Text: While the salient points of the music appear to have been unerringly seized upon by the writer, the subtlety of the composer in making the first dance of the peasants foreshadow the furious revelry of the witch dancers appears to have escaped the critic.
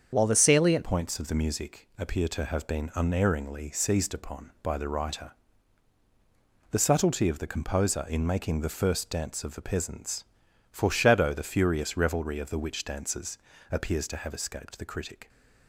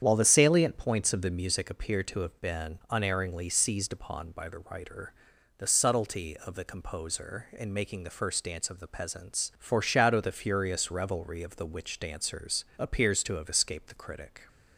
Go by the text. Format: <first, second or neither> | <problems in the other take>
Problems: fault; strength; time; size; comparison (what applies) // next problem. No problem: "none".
second | starts louder than the rest; strong; until 1.1 s; 7 dB; strong in the second // changes voice at "points"; from 0.8 s on; 14.4 s long // pauses between "peasants" and "foreshadow"; noticeable; at 10.2 s; 0.48 s long // pauses between "dancers" and "appears"; slight; at 13.3 s; 0.36 s long; slight in the second